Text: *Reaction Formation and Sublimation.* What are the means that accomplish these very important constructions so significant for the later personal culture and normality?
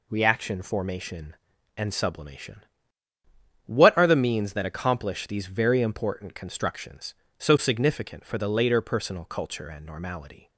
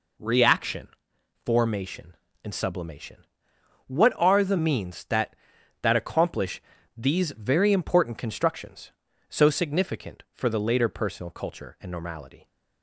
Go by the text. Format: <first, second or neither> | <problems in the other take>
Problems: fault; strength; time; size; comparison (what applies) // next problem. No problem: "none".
first | pauses between "Reaction" and "Formation"; noticeable; at 0.8 s; 0.58 s long // says "that" twice; at 5.8 s // pauses between "accomplish" and "these"; slight; at 6.6 s; 0.34 s long